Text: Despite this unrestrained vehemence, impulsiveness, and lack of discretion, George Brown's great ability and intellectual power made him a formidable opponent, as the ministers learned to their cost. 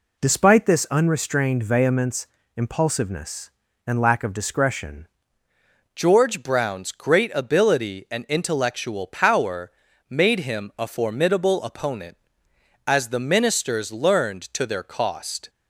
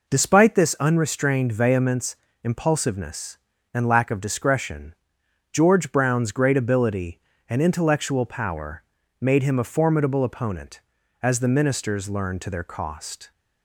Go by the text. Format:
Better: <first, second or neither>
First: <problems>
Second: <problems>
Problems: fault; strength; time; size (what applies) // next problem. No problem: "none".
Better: second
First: changes voice at "George"; from 5.9 s on; 9.5 s long // pauses between "power" and "made"; slight; at 9.7 s; 0.36 s long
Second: pauses between "power" and "made"; slight; at 8.8 s; 0.36 s long